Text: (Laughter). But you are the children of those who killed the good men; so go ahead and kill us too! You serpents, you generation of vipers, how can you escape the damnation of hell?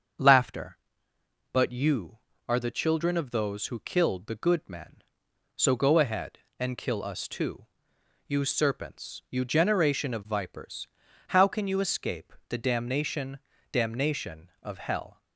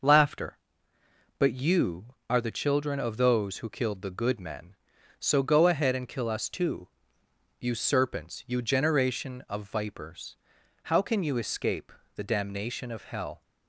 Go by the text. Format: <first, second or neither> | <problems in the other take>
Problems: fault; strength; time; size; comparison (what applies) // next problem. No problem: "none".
second | starts louder than the rest; until 2.0 s; 7 dB // pauses between "escape" and "the"; slight; at 12.3 s; 0.16 s long; slight in the second // says "damnation" twice; at 13.7 s